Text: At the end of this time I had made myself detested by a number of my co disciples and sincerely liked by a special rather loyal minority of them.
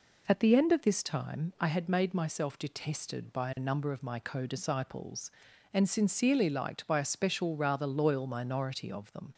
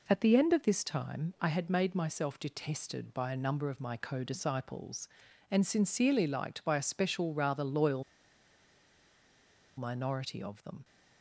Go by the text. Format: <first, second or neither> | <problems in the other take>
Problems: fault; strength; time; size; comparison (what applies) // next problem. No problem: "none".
first | pauses between "loyal" and "minority"; strong; at 8.0 s; 1.7 s long